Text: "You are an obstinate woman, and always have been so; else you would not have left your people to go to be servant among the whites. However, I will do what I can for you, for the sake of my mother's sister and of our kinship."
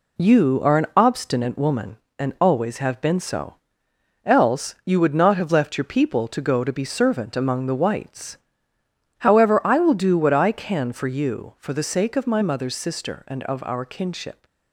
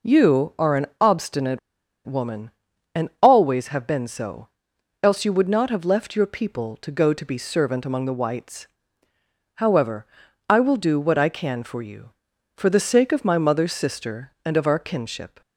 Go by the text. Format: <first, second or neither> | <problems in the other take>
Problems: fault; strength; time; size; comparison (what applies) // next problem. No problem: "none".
first | pauses between "obstinate" and "woman"; noticeable; at 1.5 s; 0.47 s long